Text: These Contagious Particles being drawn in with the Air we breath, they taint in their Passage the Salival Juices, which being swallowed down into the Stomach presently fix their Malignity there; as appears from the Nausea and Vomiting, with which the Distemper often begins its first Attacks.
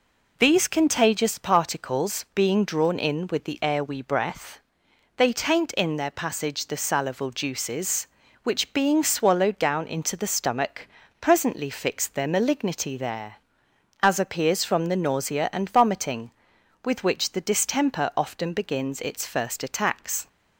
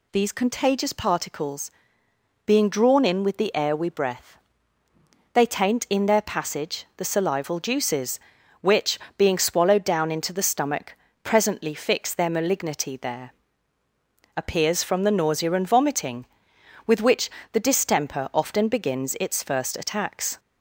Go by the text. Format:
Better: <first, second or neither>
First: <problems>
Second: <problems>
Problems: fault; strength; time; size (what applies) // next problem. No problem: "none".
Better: first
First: pauses between "Stomach" and "presently"; slight; at 10.8 s; 0.34 s long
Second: pauses between "Particles" and "being"; noticeable; at 1.6 s; 0.78 s long // pauses between "which" and "being"; slight; at 8.9 s; 0.22 s long // pauses between "Stomach" and "presently"; slight; at 10.9 s; 0.28 s long // skips "as"; at 13.8 s // pauses between "which" and "the"; slight; at 17.2 s; 0.22 s long